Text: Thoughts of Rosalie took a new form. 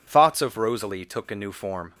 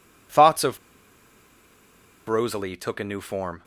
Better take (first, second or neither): first